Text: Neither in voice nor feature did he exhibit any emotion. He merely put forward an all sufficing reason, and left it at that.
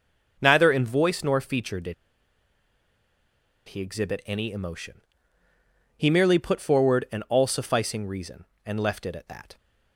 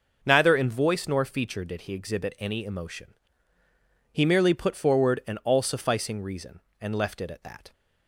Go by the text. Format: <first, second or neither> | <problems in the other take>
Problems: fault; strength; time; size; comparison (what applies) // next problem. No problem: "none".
second | pauses between "did" and "he"; strong; at 1.9 s; 1.7 s long